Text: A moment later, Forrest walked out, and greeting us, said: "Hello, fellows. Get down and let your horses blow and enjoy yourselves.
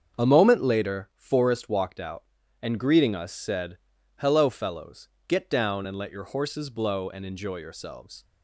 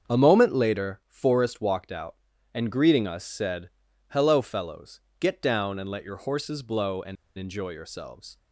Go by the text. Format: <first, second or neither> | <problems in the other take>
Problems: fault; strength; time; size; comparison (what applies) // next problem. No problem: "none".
first | starts louder than the rest; strong; until 1.1 s; 7 dB; strong in the first // pauses between "and" and "enjoy"; slight; at 7.1 s; 0.21 s long